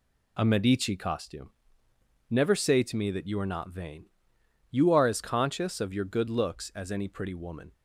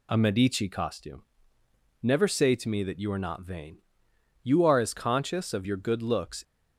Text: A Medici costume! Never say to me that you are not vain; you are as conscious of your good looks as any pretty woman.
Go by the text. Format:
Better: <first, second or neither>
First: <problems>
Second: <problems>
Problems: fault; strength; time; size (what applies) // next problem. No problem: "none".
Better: first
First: none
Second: stops before "as any pretty woman"; at 6.4 s